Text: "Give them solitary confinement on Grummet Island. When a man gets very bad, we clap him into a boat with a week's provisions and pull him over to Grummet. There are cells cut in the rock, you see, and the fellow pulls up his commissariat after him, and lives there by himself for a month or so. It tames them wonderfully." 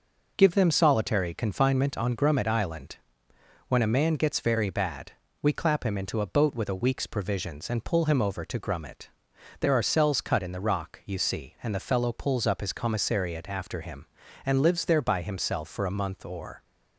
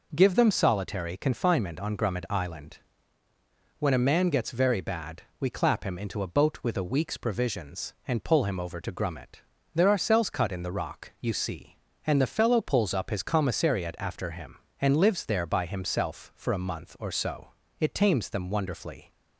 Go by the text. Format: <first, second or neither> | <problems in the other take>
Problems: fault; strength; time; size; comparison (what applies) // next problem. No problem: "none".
second | stops before "so It tames them wonderfully"; at 16.6 s